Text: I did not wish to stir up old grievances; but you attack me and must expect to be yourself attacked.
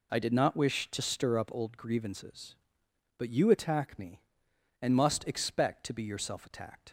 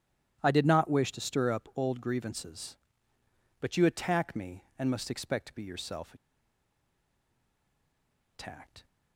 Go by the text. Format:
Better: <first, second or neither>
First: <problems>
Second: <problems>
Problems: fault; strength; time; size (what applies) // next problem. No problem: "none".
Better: first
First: none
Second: starts louder than the rest; strong; until 1.4 s; 11.5 dB // pauses between "yourself" and "attacked"; strong; at 6.1 s; 2.1 s long